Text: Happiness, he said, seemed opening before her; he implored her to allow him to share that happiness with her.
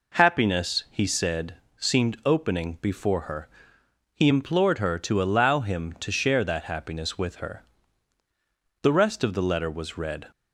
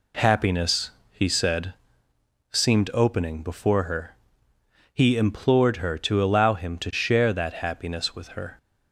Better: second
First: goes on to say "The rest of the letter was read"; from 8.8 s on; 1.4 s long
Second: none

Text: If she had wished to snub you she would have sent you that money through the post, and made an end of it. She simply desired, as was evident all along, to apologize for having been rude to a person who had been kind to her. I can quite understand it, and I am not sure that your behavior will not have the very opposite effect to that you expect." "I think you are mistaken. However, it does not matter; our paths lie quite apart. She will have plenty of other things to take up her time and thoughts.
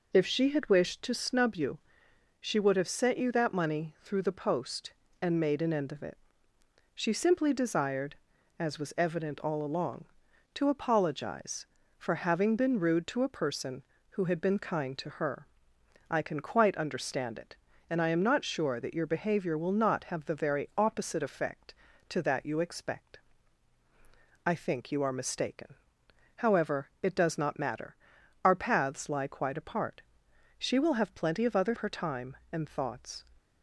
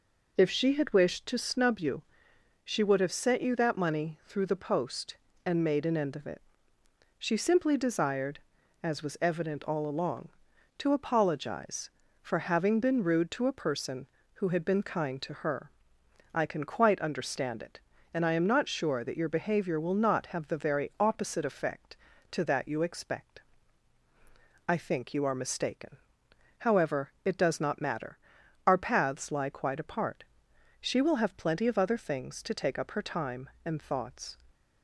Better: second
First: pauses between "you" and "she"; noticeable; at 1.7 s; 0.64 s long // skips "things to take up"; at 31.7 s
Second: pauses between "you" and "she"; noticeable; at 2.0 s; 0.64 s long

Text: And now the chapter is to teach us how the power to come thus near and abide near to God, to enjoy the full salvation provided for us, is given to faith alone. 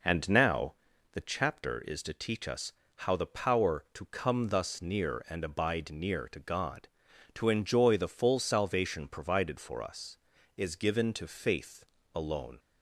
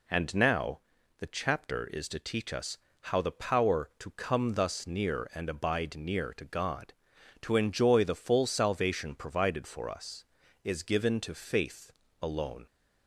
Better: second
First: starts louder than the rest; noticeable; until 1.5 s; 5 dB // pauses between "now" and "the"; at 0.7 s; 0.40 s long // pauses between "us" and "how"; slight; at 2.7 s; 0.24 s long // pauses between "faith" and "alone"; slight; at 11.8 s; 0.28 s long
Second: pauses between "now" and "the"; at 0.7 s; 0.40 s long // pauses between "us" and "how"; slight; at 2.7 s; 0.24 s long // pauses between "faith" and "alone"; slight; at 11.9 s; 0.28 s long

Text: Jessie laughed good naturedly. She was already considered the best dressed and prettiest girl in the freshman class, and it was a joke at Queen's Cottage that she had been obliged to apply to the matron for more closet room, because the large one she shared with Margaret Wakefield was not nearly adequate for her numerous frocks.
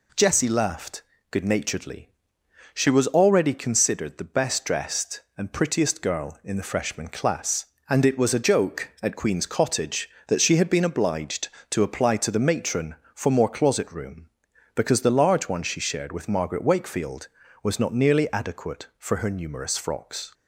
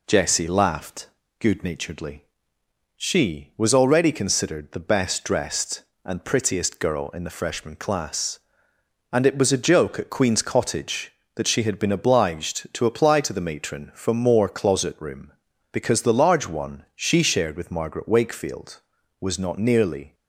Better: first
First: pauses between "laughed" and "good"; slight; at 1.0 s; 0.28 s long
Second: pauses between "laughed" and "good"; slight; at 1.0 s; 0.32 s long // stops before "adequate for her numerous frocks"; at 20.1 s

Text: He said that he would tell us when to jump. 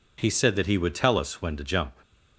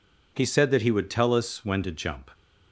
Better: neither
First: none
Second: none

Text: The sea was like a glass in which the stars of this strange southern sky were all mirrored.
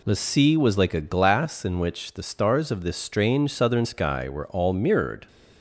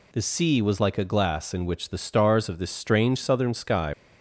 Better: first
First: none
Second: stops before "were all mirrored"; at 3.9 s

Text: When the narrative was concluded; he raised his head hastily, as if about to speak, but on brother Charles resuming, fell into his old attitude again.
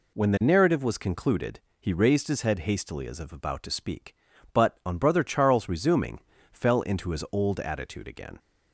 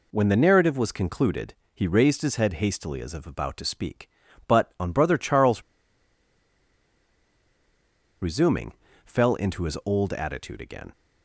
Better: first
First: none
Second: pauses between "Charles" and "resuming"; strong; at 5.6 s; 2.5 s long

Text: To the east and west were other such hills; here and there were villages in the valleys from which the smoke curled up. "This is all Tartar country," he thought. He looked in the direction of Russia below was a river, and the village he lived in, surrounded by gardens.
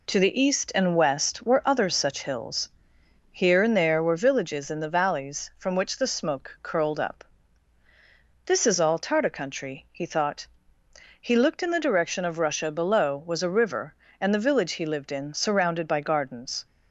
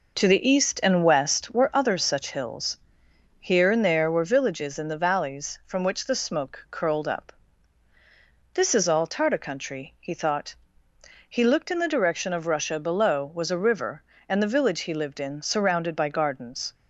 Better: first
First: none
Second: starts louder than the rest; noticeable; until 1.6 s; 5 dB

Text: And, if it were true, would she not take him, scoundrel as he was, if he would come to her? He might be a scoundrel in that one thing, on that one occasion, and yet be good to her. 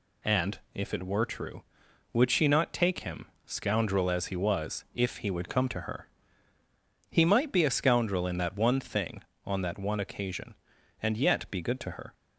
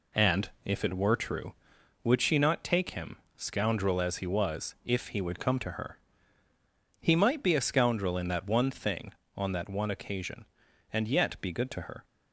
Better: first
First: none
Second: starts louder than the rest; slight; until 1.8 s; 2.5 dB

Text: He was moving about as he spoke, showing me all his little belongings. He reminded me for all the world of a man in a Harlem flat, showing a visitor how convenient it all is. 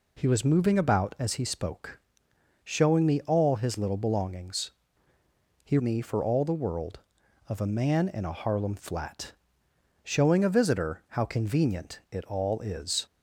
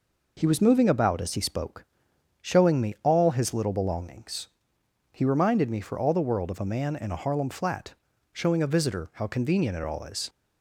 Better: second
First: skips "reminded"; at 5.7 s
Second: none

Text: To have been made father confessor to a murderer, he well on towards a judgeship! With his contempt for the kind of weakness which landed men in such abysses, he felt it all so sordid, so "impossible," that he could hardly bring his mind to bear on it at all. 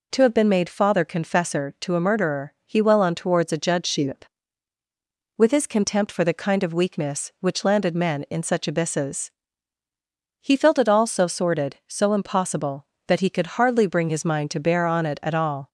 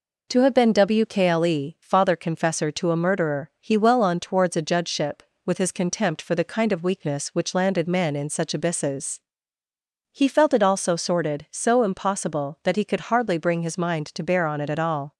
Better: first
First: none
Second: says "wkle" for "made"; at 0.7 s

